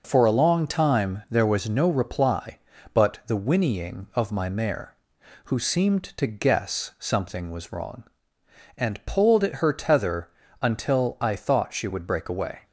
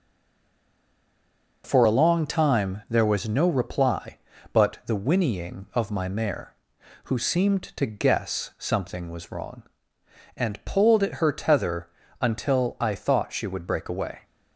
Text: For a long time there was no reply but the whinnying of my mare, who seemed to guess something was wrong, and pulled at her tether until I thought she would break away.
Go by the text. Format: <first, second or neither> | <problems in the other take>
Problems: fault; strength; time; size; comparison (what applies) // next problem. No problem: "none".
first | stays silent before the first word; noticeable; until 1.6 s; 1.6 s long // pauses between "tether" and "until"; slight; at 11.8 s; 0.32 s long; slight in the first